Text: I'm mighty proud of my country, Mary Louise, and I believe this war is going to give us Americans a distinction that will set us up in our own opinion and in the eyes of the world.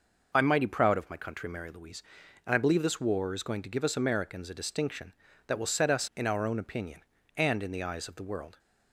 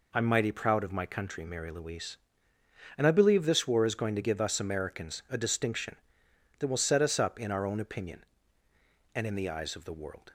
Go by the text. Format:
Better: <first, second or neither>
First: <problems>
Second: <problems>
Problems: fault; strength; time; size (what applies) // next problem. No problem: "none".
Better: second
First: skips "up"; at 6.1 s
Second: none